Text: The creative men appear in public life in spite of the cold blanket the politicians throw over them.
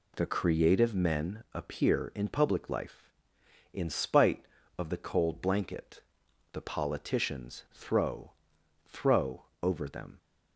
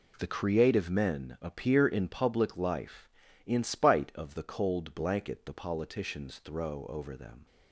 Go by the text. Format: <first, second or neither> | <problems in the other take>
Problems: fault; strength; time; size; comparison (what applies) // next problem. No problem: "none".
second | pauses between "blanket" and "the"; noticeable; at 6.0 s; 0.52 s long // says "throw" twice; at 8.8 s